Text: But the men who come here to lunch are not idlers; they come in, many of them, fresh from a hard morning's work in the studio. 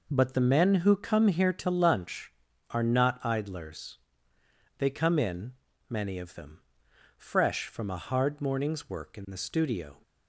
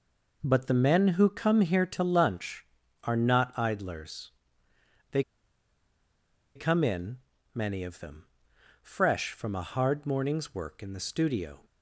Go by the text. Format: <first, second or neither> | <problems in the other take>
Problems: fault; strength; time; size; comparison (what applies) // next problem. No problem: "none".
first | pauses between "they" and "come"; strong; at 5.2 s; 1.3 s long